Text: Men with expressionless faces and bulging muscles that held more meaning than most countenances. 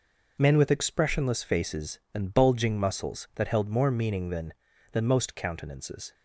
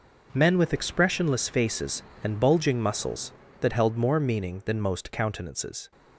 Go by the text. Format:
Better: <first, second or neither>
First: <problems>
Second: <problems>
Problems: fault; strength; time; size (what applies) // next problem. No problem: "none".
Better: second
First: says "than" twice; at 4.9 s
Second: none